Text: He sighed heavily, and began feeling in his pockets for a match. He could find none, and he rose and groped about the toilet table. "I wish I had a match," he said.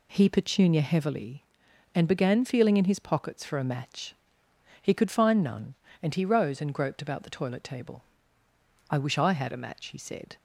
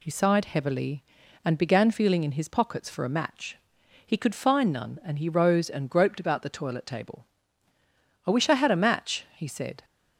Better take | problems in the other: second | says "petunia" for "sighed"; at 0.2 s

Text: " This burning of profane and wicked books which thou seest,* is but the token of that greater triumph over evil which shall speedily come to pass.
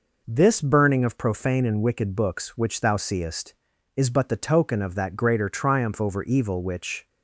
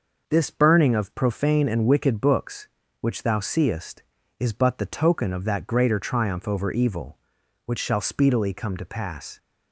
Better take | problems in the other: second | stops before "shall speedily come to pass"; at 7.0 s

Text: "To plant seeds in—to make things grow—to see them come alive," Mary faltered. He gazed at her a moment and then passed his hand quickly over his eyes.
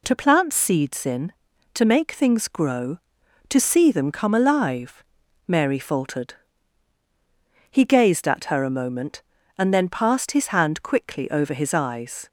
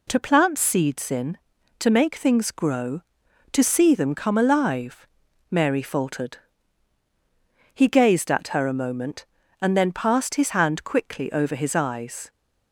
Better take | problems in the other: neither | none

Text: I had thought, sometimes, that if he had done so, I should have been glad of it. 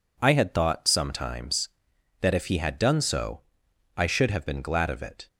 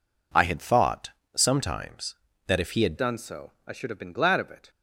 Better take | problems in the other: first | changes voice at "done"; from 2.9 s on; 1.7 s long

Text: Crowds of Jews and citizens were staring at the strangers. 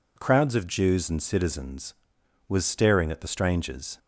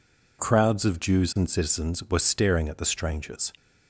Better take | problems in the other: second | says "was" for "were"; at 2.4 s

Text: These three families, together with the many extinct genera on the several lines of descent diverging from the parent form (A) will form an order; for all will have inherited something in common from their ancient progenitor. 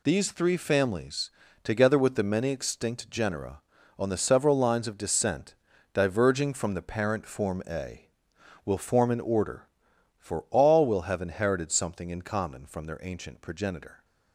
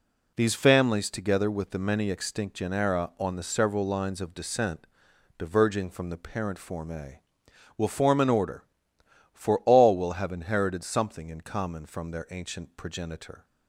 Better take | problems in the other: first | skips "three"; at 0.5 s // pauses between "descent" and "diverging"; noticeable; at 4.8 s; 0.50 s long; also in the first

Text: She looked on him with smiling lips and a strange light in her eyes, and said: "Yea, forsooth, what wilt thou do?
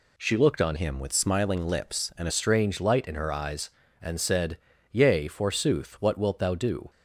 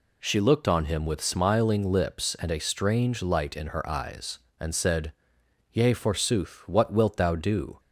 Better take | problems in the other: second | changes voice from "him" to "a"; from 0.7 to 2.3 s; 1.6 s long

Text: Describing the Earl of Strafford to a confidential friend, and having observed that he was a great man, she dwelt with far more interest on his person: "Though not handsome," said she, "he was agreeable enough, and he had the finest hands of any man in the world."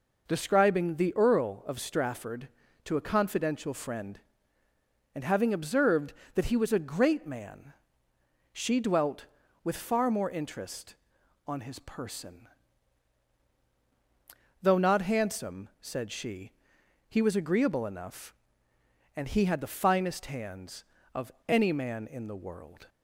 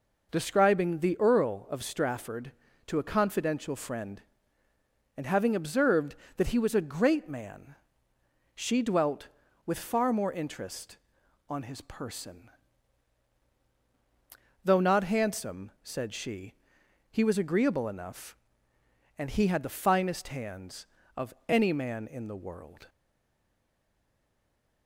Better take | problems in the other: first | pauses between "of" and "any"; slight; at 21.3 s; 0.16 s long; slight in the first // stays silent after the last word; noticeable; from 22.8 s on; 2.0 s long

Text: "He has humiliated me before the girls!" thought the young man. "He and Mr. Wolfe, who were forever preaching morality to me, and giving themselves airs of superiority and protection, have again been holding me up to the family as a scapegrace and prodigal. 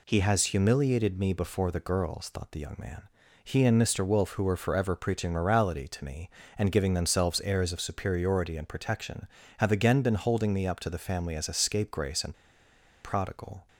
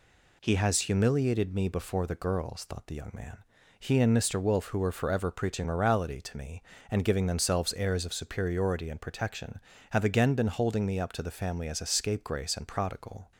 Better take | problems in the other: second | pauses between "and" and "prodigal"; noticeable; at 12.3 s; 0.69 s long

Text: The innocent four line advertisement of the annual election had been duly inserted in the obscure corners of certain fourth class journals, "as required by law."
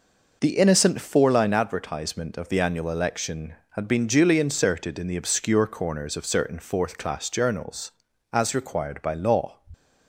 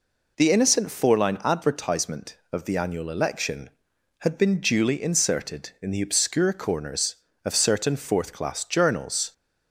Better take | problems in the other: first | stops before "as required by law"; at 9.3 s

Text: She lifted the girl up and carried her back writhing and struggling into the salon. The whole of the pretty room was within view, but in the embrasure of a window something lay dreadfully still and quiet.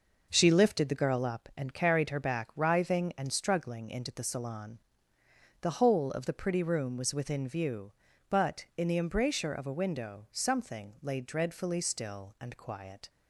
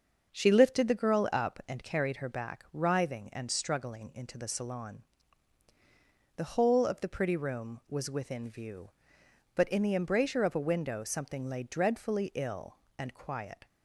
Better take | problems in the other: first | starts louder than the rest; until 1.3 s; 6.5 dB // says "ill" for "still"; at 12.3 s

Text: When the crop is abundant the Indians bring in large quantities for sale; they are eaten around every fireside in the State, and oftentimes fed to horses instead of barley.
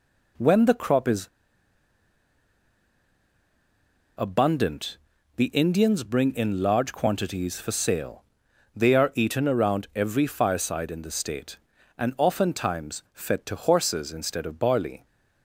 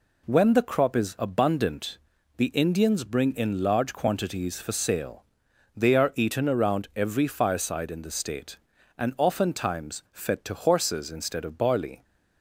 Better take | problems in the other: second | pauses between "is" and "abundant"; strong; at 1.2 s; 2.9 s long // pauses between "abundant" and "the"; at 4.9 s; 0.40 s long; also in the second

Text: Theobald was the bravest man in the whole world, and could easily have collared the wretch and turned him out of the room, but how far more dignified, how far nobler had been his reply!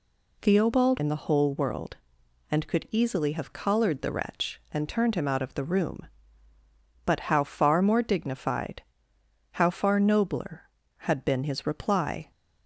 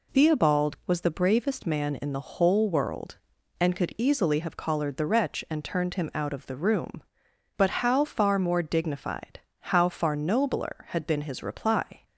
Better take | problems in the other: second | skips "was the bravest man"; at 0.9 s

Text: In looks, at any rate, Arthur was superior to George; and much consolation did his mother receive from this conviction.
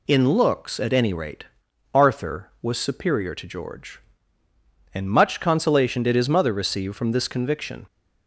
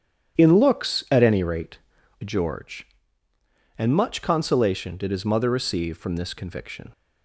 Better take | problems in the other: first | starts louder than the rest; strong; until 1.4 s; 9.5 dB // skips "Arthur was superior to"; at 2.0 s

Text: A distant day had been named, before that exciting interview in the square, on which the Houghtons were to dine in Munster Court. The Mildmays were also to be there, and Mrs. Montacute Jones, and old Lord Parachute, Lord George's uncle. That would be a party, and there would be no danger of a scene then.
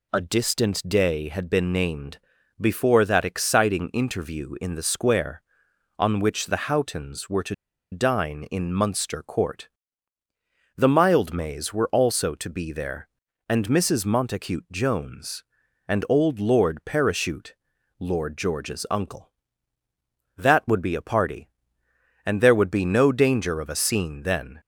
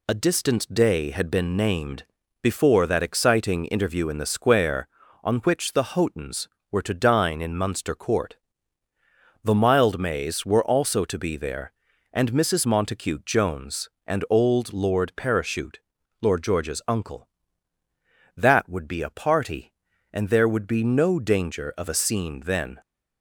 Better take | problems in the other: second | pauses between "to" and "dine"; at 7.5 s; 0.37 s long

